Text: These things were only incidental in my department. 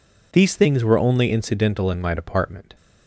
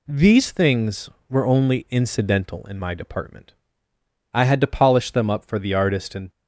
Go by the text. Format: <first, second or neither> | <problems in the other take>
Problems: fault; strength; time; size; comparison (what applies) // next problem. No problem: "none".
first | goes on to say "I had to polish them up for the artist and"; strong; from 4.3 s on; 1.9 s long